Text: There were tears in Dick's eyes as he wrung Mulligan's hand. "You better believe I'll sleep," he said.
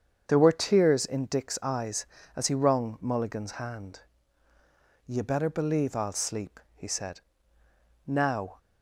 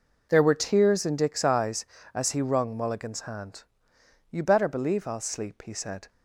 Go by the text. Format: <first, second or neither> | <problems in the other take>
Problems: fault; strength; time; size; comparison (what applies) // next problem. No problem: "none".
second | starts louder than the rest; strong; until 1.2 s; 7.5 dB // goes on to say "Now"; from 8.0 s on; 0.50 s long